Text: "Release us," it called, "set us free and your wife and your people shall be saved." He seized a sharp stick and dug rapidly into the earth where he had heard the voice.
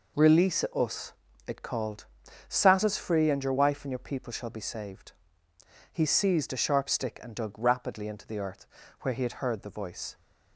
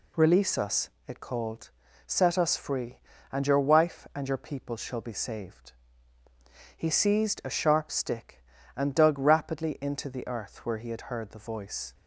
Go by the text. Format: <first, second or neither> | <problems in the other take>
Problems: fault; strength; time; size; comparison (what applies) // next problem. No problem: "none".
second | says "sat" for "set"; at 2.4 s // pauses between "earth" and "where"; slight; at 8.6 s; 0.36 s long